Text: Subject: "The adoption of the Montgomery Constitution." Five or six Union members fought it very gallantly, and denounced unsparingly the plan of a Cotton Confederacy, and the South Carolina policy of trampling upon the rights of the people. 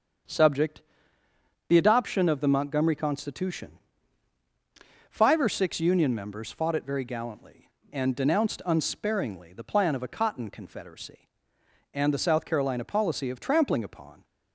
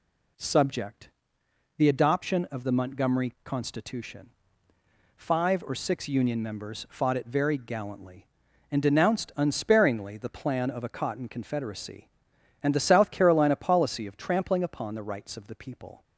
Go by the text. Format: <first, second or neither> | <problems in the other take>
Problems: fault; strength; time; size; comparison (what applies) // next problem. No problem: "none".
second | starts louder than the rest; until 2.1 s; 7 dB // stops before "the rights of the people"; at 14.2 s